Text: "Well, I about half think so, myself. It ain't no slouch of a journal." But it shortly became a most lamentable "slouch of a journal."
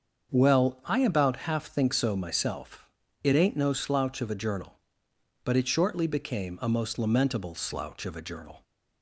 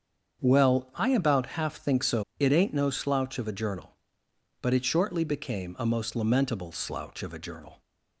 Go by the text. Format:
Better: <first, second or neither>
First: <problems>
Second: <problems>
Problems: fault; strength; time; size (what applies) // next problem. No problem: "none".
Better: first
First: starts louder than the rest; until 1.3 s; 7 dB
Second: starts louder than the rest; strong; until 1.4 s; 7.5 dB // skips "myself"; at 2.3 s